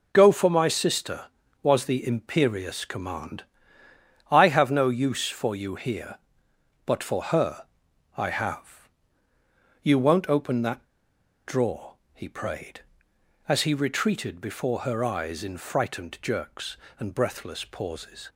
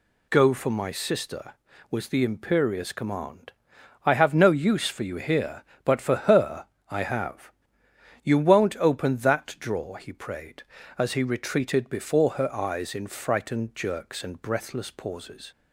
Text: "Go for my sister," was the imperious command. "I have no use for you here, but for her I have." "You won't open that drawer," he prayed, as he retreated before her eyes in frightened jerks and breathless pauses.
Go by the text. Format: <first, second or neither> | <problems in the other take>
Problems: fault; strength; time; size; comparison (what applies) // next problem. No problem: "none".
second | pauses between "her" and "I"; noticeable; at 7.6 s; 0.50 s long; slight in the second // pauses between "that" and "drawer"; noticeable; at 10.8 s; 0.61 s long